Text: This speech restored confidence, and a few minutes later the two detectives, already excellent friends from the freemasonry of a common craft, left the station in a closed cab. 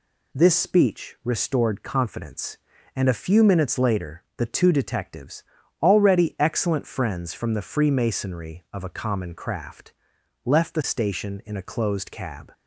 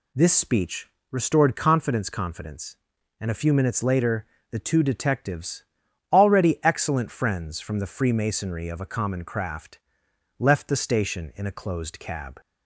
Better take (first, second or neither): first